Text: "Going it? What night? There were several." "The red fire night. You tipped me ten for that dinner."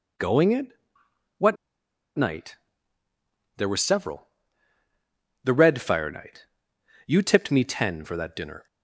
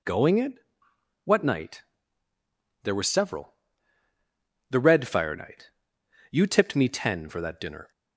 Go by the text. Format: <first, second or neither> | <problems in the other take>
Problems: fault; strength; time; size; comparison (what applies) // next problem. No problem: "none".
second | pauses between "What" and "night"; noticeable; at 1.5 s; 0.62 s long